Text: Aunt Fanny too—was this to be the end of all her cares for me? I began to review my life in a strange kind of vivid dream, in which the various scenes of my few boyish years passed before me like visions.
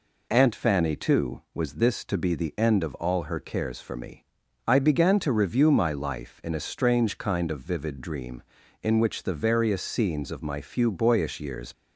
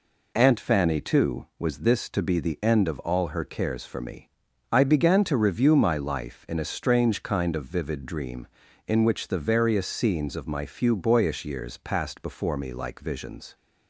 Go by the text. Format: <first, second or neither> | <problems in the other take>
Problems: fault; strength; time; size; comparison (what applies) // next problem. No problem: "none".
second | stops before "passed before me like visions"; at 11.7 s